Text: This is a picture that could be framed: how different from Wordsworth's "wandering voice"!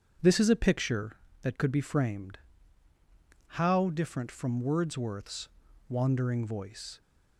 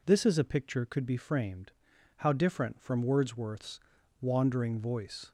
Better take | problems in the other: first | skips "that"; at 0.8 s // pauses between "Wordsworth's" and "wandering"; at 3.7 s; 0.40 s long; also in the first

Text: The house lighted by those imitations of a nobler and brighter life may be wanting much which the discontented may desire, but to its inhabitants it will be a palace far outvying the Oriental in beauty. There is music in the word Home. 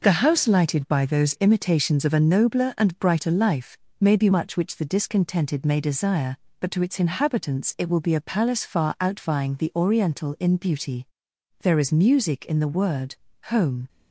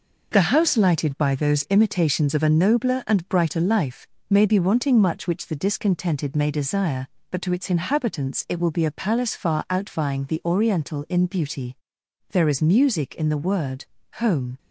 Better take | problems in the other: second | pauses between "life" and "may"; slight; at 3.7 s; 0.24 s long; slight in the second // skips "wanting"; at 4.2 s // pauses between "word" and "Home"; slight; at 13.1 s; 0.36 s long; slight in the second

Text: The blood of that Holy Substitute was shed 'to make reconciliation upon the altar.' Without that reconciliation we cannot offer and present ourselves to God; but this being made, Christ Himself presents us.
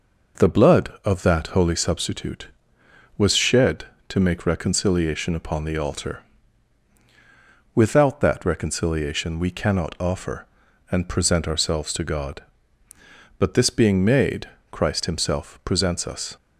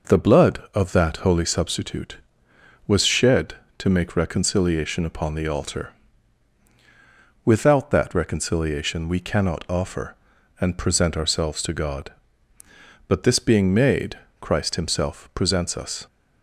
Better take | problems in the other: neither | none

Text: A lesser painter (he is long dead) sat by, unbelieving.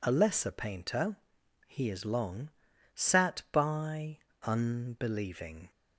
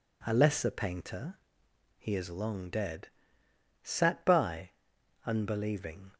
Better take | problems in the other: second | skips "dead"; at 2.7 s

